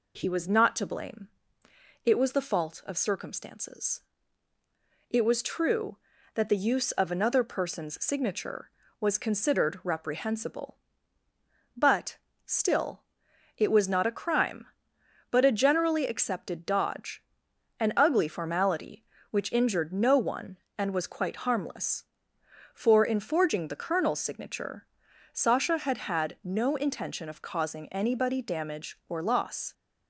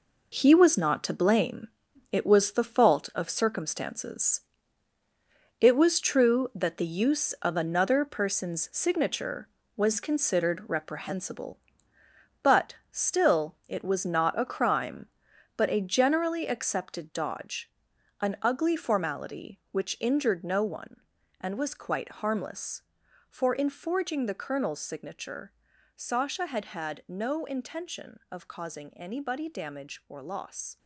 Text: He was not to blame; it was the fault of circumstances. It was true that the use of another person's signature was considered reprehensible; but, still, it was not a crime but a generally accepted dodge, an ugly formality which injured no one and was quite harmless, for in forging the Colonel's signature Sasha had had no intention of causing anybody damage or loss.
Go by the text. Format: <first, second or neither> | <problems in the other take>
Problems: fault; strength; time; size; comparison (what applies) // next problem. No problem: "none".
first | gets quieter; strong; throughout; 10 dB // pauses between "signature" and "Sasha"; at 25.5 s; 0.42 s long; noticeable in the first